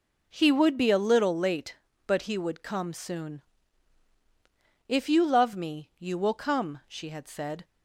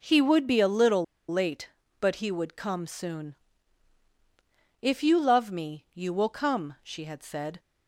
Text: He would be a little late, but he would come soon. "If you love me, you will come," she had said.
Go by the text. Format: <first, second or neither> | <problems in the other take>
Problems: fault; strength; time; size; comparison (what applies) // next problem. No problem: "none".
first | pauses between "little" and "late"; slight; at 1.0 s; 0.26 s long